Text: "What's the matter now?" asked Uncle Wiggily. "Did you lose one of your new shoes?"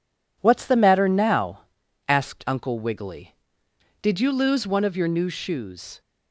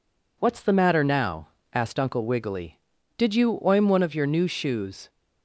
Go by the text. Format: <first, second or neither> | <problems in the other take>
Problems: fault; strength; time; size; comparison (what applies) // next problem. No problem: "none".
first | says "oim" for "lose"; at 3.6 s